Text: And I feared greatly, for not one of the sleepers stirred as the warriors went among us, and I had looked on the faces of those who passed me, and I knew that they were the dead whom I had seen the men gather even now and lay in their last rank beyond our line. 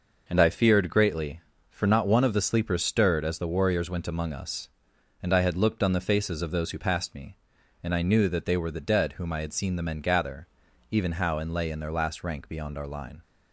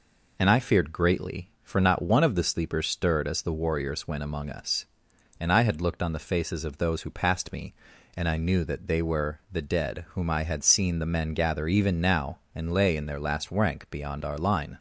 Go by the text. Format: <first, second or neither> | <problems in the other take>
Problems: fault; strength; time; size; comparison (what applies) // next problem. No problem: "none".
second | pauses between "gather" and "even"; at 10.4 s; 0.44 s long // says "how" for "now"; at 11.1 s